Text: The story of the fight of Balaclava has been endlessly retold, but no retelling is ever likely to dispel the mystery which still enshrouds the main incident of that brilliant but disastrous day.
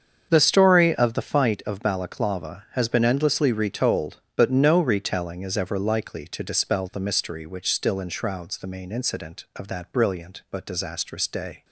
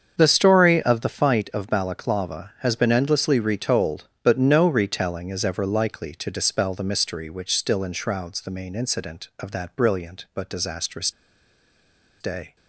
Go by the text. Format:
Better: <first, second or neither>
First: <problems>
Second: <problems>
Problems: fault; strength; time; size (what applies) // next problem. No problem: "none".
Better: first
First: starts louder than the rest; strong; until 1.3 s; 7 dB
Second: starts louder than the rest; strong; until 1.1 s; 7 dB // pauses between "disastrous" and "day"; at 11.0 s; 1.1 s long